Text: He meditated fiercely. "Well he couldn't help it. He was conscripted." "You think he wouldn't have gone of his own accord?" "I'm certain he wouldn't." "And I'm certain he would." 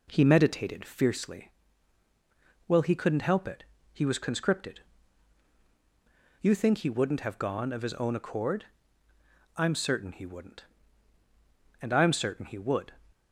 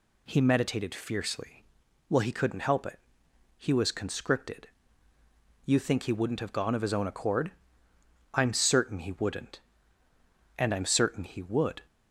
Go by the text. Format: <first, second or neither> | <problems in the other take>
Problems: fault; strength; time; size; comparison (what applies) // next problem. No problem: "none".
second | starts louder than the rest; until 1.1 s; 4 dB